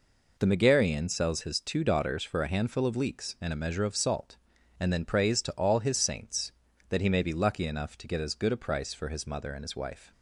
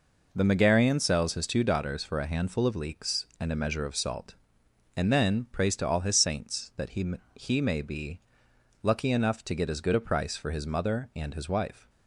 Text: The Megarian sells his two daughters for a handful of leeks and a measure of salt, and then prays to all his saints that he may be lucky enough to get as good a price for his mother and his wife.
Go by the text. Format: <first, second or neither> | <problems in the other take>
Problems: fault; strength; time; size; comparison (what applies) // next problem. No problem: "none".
first | says "he" twice; at 7.3 s // pauses between "be" and "lucky"; noticeable; at 8.2 s; 0.60 s long